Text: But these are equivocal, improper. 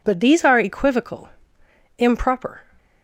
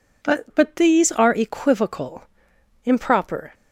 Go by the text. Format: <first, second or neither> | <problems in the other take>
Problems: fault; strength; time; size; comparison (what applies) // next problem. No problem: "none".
first | says "But" twice; at 0.5 s